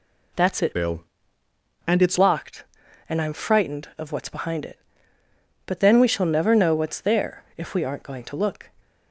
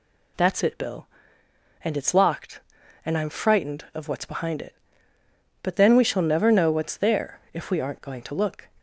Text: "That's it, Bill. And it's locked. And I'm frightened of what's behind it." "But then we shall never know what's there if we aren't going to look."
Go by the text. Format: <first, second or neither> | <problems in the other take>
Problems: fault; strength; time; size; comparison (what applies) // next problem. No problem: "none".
second | changes voice from "Bill" to "it's"; from 0.7 to 2.1 s; 1.4 s long